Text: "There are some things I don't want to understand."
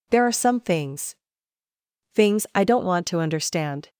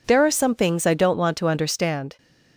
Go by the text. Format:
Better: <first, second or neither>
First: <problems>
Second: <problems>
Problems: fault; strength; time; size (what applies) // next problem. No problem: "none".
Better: second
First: says "things" twice; at 2.1 s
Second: none